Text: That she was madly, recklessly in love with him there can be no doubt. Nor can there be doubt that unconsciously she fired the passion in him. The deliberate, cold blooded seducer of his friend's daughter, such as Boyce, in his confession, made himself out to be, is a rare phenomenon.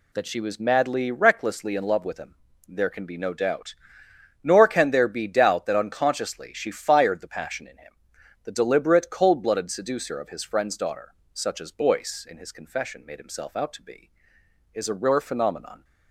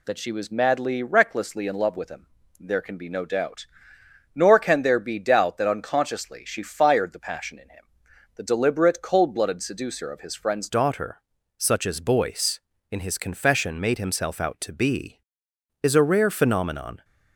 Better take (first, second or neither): first